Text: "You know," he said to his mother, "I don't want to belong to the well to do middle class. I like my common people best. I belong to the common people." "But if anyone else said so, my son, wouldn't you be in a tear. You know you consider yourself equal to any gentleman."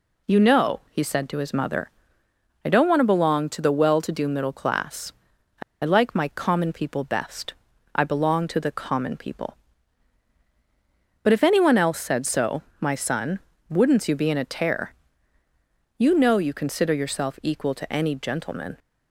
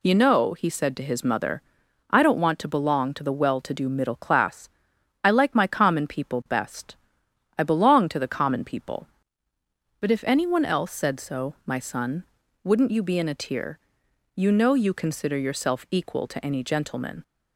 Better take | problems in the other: second | pauses between "I" and "like"; slight; at 5.6 s; 0.21 s long

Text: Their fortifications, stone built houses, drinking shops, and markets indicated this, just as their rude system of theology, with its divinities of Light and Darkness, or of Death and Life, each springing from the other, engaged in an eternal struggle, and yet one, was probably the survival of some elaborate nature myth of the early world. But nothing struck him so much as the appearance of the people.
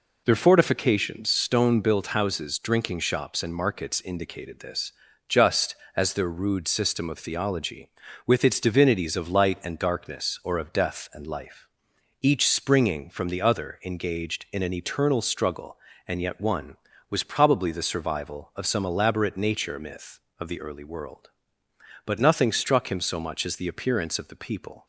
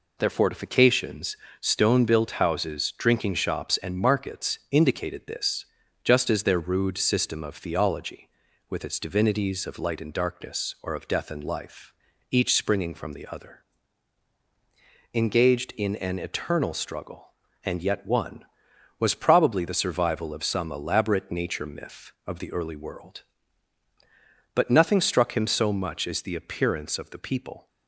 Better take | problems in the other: neither | none

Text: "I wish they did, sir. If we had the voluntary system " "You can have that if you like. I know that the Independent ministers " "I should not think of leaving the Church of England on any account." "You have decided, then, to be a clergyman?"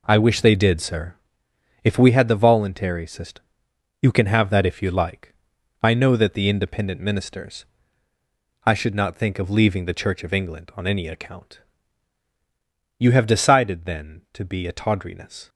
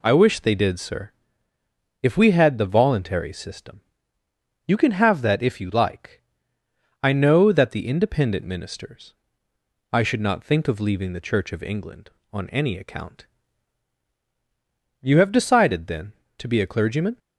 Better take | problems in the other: second | says "tawdriness" for "clergyman"; at 14.7 s

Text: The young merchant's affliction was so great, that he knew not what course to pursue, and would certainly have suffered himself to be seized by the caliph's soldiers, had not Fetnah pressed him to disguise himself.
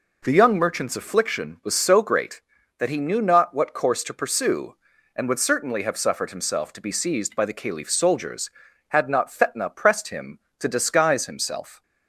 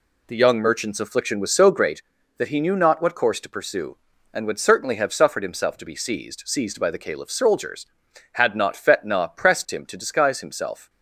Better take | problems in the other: first | says "seized" twice; at 6.4 s

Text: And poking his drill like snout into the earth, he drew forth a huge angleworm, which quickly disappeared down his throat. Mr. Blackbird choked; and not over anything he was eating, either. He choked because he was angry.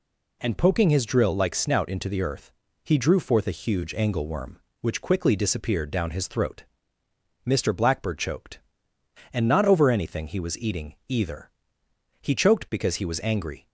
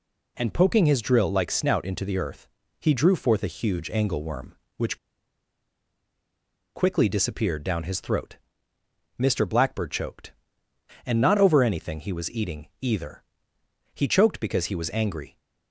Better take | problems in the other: first | pauses between "which" and "quickly"; strong; at 4.9 s; 1.7 s long

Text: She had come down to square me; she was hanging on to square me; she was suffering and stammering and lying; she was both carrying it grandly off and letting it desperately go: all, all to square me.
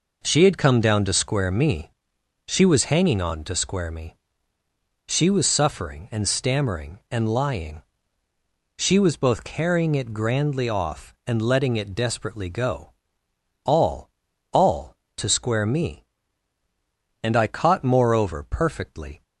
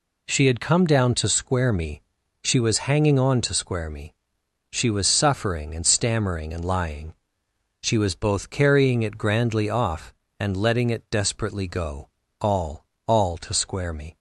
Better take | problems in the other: second | goes on to say "And I caught moreover perfectly"; strong; from 17.2 s on; 2.0 s long

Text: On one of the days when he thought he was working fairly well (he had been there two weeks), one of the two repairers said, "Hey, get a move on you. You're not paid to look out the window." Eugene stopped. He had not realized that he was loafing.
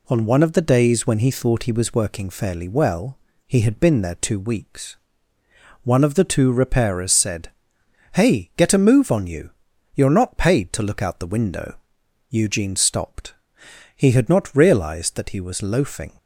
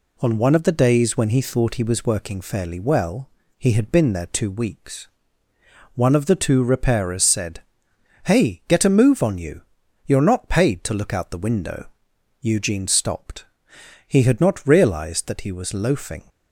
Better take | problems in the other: neither | none

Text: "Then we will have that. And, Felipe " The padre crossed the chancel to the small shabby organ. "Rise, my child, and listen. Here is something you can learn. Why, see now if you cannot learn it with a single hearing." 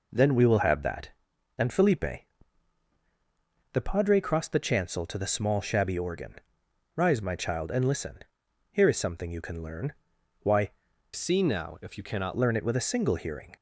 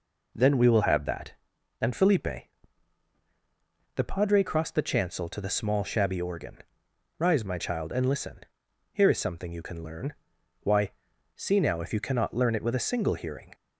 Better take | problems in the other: second | changes voice from "see" to "cannot"; from 11.1 to 12.3 s; 1.2 s long

